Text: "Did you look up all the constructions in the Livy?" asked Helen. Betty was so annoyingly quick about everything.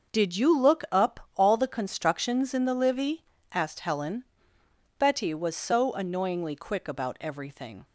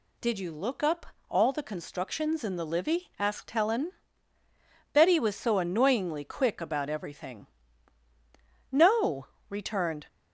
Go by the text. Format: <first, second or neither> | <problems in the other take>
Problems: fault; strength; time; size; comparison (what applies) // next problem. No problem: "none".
first | pauses between "up" and "all"; slight; at 1.0 s; 0.24 s long // goes on to say "No returned"; from 8.7 s on; 1.3 s long